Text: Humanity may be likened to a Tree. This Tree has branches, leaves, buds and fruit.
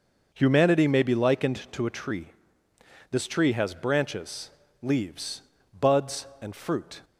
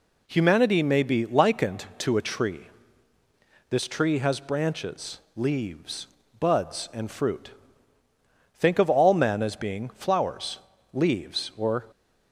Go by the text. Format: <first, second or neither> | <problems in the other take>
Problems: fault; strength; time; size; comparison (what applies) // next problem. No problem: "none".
first | goes on to say "Think of all men as being flowers leaves or"; strong; from 8.5 s on; 3.2 s long